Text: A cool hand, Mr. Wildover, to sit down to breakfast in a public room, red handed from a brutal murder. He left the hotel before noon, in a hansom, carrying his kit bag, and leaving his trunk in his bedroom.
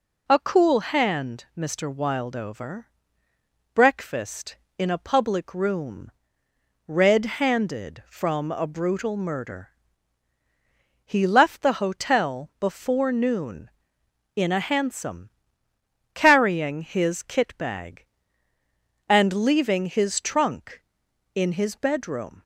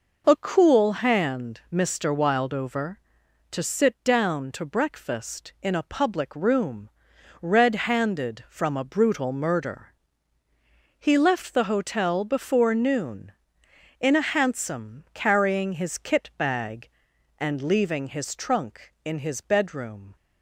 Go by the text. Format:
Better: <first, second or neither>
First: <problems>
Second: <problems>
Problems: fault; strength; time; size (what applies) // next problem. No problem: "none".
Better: second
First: skips "to sit down to"; at 3.2 s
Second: none